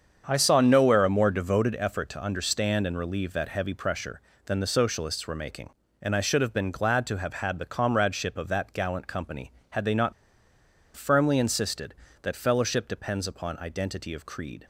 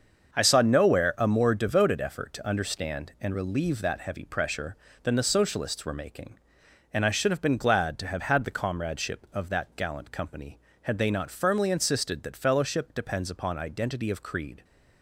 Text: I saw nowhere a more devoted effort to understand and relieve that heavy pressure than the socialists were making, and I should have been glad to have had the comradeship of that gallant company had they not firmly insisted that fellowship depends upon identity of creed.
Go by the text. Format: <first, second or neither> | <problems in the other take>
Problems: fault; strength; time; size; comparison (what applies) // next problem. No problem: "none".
second | starts louder than the rest; strong; until 1.2 s; 7.5 dB; also in the second // pauses between "not" and "firmly"; noticeable; at 10.1 s; 0.82 s long